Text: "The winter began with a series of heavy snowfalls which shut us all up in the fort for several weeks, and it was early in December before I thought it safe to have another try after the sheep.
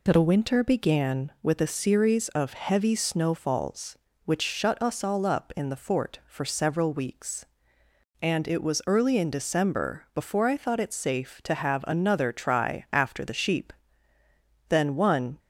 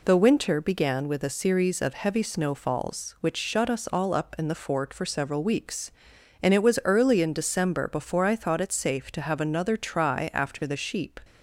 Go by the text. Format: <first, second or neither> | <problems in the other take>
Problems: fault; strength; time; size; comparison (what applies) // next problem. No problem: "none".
second | goes on to say "Then one"; noticeable; from 14.6 s on; 0.70 s long